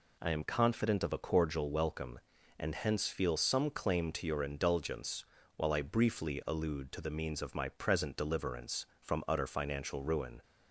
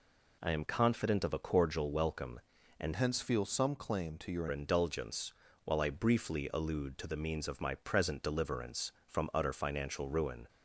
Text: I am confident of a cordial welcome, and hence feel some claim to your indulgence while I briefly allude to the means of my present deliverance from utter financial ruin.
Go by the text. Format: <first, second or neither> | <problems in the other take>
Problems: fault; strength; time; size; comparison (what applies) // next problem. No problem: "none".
first | changes voice from "hence" to "your"; from 2.9 to 4.4 s; 1.5 s long // pauses between "indulgence" and "while"; slight; at 5.3 s; 0.32 s long; slight in the first